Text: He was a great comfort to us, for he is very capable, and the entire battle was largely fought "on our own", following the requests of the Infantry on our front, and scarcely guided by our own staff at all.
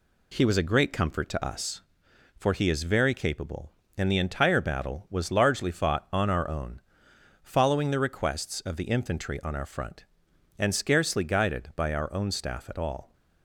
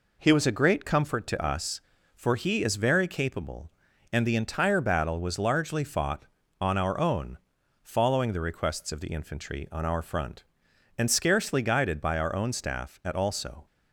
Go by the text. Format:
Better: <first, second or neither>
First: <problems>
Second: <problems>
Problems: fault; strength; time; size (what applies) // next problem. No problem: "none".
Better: first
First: none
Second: says "also" for "all"; at 13.1 s